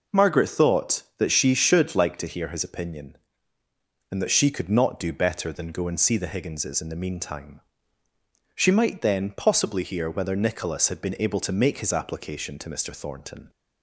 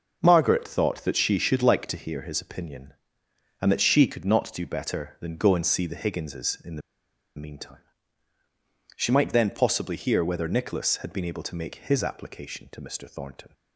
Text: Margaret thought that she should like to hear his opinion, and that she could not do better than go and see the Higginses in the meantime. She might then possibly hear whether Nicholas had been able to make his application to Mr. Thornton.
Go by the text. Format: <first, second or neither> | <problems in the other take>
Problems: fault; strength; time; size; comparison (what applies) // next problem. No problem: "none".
first | starts louder than the rest; noticeable; until 1.2 s; 6 dB // pauses between "the" and "meantime"; noticeable; at 6.8 s; 0.55 s long